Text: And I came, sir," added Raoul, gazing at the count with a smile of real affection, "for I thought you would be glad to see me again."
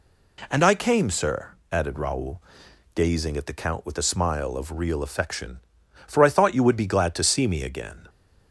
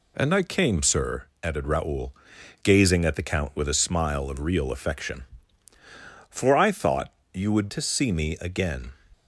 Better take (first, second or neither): first